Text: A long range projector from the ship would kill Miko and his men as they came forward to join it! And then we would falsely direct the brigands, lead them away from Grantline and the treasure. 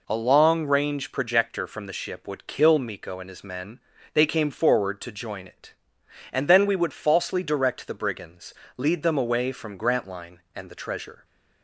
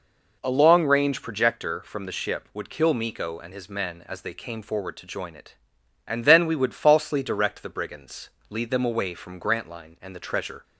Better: second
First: skips "as"; at 3.9 s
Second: none

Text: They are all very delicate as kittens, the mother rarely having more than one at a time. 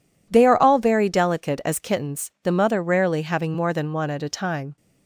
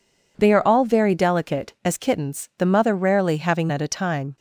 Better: first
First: none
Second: skips "more than one"; at 3.7 s

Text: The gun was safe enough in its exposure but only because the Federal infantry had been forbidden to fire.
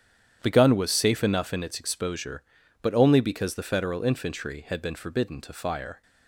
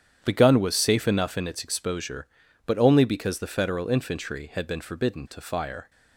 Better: neither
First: starts louder than the rest; strong; until 1.4 s; 9.5 dB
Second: starts louder than the rest; strong; until 1.2 s; 9.5 dB

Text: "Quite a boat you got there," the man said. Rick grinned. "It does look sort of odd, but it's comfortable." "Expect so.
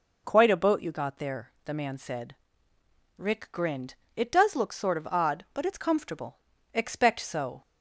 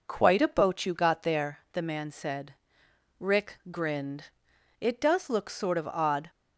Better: first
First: none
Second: stops before "but it's comfortable Expect so"; at 6.2 s

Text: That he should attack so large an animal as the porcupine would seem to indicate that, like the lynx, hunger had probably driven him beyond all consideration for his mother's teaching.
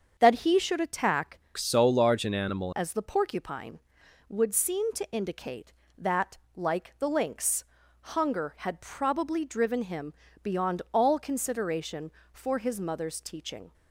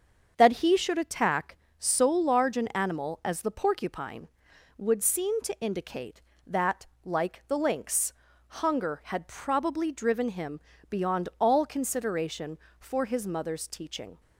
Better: second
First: starts louder than the rest; until 1.1 s; 7 dB // changes voice from "so" to "animal"; from 1.5 to 2.7 s; 1.2 s long // pauses between "him" and "beyond"; slight; at 10.1 s; 0.28 s long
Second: starts louder than the rest; until 1.3 s; 7 dB // pauses between "him" and "beyond"; slight; at 10.5 s; 0.28 s long

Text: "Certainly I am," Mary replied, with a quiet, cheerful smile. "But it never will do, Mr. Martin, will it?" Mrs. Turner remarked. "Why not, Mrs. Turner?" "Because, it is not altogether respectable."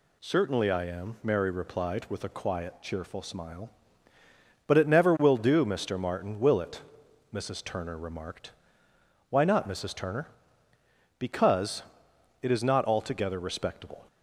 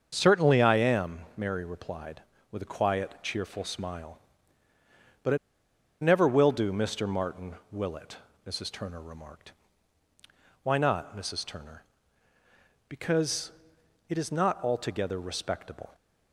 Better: first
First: none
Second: starts louder than the rest; until 1.1 s; 7 dB // pauses between "it" and "never"; noticeable; at 5.3 s; 0.65 s long

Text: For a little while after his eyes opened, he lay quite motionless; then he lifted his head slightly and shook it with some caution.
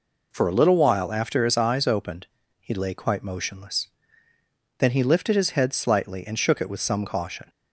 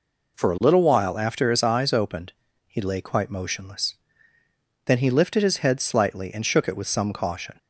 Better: neither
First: none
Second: none

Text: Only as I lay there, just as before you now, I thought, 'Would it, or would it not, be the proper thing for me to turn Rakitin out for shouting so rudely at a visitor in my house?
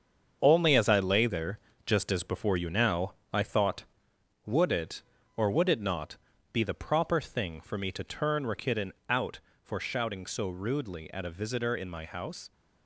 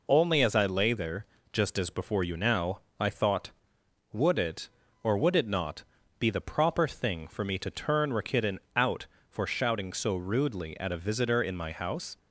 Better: second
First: gets quieter; strong; throughout; 8.5 dB // pauses between "Rakitin" and "out"; slight; at 8.9 s; 0.16 s long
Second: pauses between "Rakitin" and "out"; slight; at 8.5 s; 0.16 s long

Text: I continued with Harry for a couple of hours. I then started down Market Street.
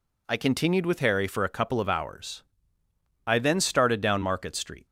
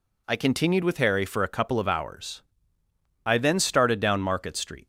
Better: neither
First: none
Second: none

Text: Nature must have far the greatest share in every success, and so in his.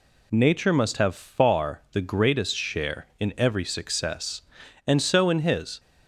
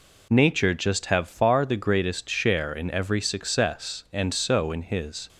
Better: first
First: none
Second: says "just" for "must"; at 0.7 s

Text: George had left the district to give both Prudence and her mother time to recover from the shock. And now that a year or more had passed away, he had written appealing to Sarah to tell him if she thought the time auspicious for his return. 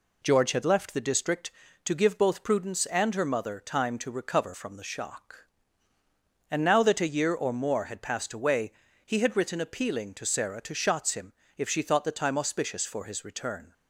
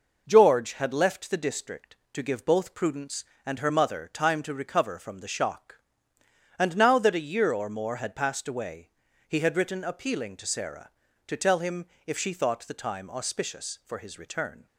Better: second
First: says "shots" for "tell"; at 10.7 s // pauses between "him" and "if"; slight; at 11.3 s; 0.24 s long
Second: pauses between "him" and "if"; slight; at 11.8 s; 0.20 s long

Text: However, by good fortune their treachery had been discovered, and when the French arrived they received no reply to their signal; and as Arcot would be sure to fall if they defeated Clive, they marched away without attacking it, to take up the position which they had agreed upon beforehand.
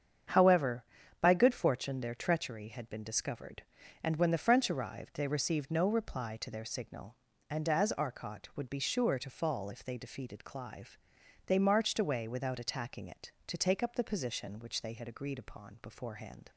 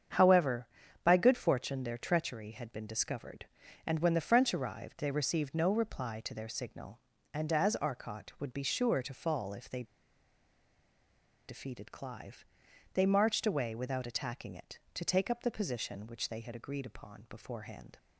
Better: first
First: starts louder than the rest; strong; until 1.6 s; 8 dB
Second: starts louder than the rest; strong; until 1.5 s; 8 dB // pauses between "they" and "defeated"; strong; at 9.8 s; 1.6 s long

